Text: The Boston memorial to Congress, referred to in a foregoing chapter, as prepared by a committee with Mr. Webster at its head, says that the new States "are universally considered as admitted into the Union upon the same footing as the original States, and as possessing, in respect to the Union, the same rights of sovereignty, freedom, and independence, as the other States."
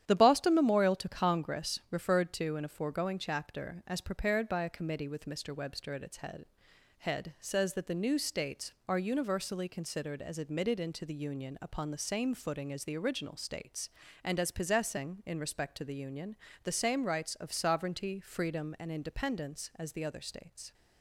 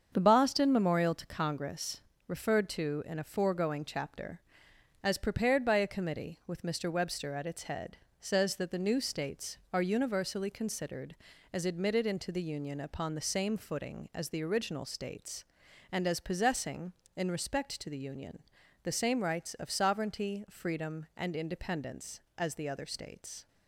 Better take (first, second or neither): second